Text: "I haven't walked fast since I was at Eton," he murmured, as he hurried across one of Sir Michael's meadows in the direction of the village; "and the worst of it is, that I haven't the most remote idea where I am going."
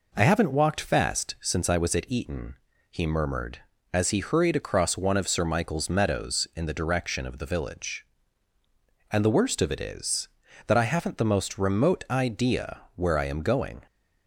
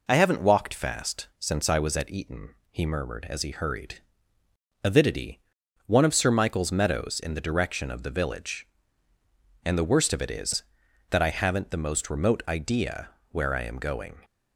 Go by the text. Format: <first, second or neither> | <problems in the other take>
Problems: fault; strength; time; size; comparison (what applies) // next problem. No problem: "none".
first | says "avidity" for "across"; at 4.8 s // pauses between "idea" and "where"; slight; at 13.1 s; 0.20 s long; slight in the first